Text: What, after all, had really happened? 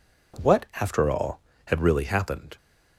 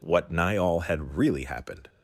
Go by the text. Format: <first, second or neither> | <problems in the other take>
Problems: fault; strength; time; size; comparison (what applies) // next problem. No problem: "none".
first | says "nigh" for "after"; at 0.3 s